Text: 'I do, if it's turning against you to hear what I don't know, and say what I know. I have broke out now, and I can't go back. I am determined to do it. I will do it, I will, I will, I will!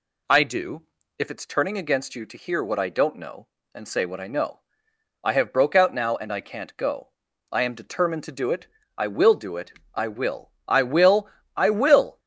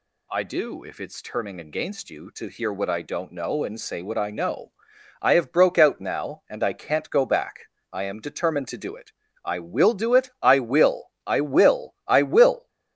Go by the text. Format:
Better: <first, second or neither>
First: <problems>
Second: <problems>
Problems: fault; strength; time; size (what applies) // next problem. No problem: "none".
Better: second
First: skips "back"; at 7.3 s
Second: none